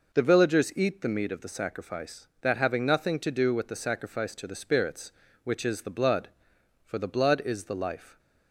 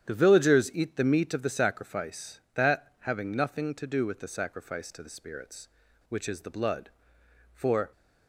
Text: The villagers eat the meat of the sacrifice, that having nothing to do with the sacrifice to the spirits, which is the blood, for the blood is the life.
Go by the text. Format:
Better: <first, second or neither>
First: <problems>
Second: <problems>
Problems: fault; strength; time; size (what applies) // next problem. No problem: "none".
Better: first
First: none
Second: starts louder than the rest; strong; until 1.0 s; 9 dB // stops before "the blood is the life"; at 7.9 s